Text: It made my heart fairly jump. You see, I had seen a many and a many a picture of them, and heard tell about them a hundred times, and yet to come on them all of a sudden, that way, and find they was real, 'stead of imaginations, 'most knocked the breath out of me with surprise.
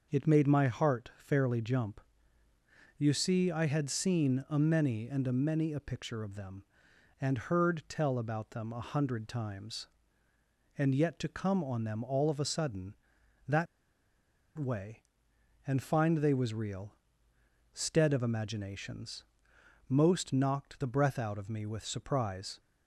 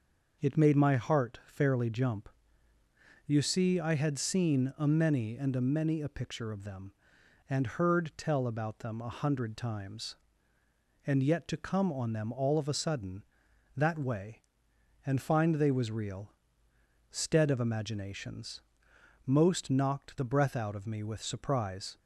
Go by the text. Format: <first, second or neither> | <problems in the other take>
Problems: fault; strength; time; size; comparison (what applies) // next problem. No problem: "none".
second | pauses between "that" and "way"; noticeable; at 13.6 s; 0.91 s long